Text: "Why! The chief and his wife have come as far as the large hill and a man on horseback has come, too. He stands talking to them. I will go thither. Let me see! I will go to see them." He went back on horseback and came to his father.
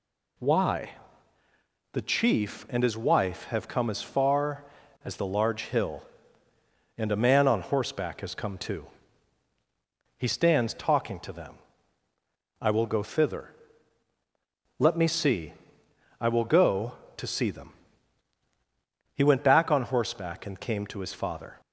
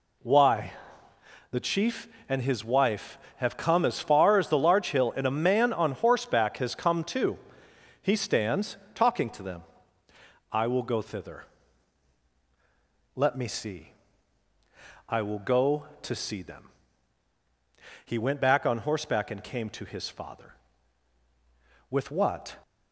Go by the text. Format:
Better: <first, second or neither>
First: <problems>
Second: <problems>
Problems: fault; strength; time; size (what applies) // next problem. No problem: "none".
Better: first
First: none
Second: pauses between "stands" and "talking"; slight; at 8.7 s; 0.18 s long // goes on to say "With what"; noticeable; from 21.9 s on; 0.66 s long